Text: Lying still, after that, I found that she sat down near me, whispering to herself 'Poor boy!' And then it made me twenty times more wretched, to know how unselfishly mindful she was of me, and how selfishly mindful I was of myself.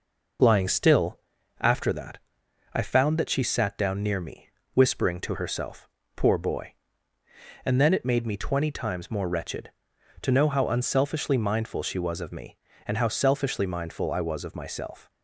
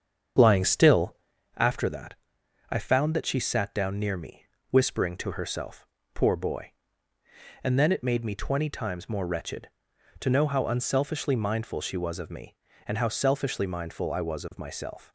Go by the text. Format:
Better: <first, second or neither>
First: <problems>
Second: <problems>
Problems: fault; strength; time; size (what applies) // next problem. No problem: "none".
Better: first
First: pauses between "herself" and "Poor"; slight; at 5.8 s; 0.26 s long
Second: starts louder than the rest; strong; until 1.4 s; 7.5 dB // pauses between "herself" and "Poor"; slight; at 5.8 s; 0.26 s long